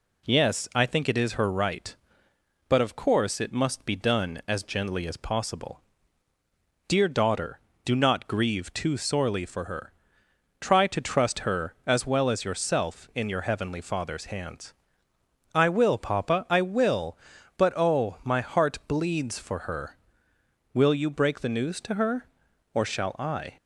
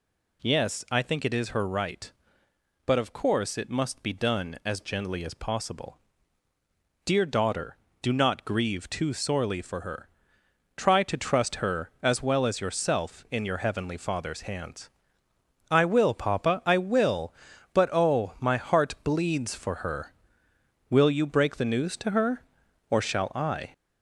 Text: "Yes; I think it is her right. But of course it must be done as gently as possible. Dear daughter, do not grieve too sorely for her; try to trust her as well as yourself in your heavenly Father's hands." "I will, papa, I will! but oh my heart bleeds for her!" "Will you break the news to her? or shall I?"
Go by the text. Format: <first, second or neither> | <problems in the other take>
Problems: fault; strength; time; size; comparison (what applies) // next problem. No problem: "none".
first | gets louder; noticeable; throughout; 4 dB